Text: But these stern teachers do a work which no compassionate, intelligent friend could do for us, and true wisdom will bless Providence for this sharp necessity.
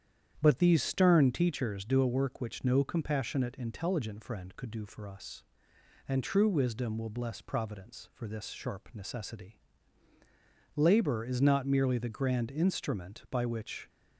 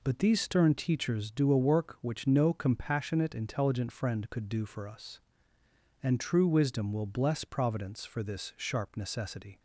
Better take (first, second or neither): second